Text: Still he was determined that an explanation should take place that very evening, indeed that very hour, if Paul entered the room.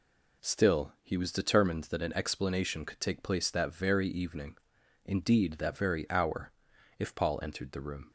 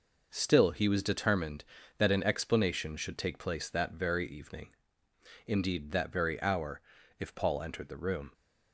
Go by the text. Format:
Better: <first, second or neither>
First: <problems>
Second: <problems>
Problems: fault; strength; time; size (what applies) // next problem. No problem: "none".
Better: second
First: says "could" for "should"; at 2.8 s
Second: none